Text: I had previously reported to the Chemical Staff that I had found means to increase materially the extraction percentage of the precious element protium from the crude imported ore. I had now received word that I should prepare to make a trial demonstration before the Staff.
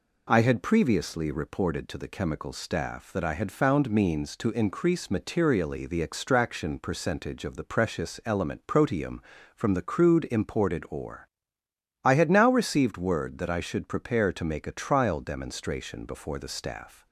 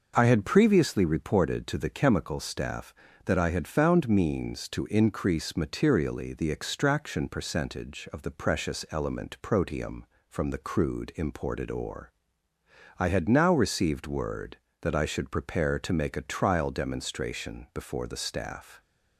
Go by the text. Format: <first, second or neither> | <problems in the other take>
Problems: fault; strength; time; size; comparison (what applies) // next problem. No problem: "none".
neither | none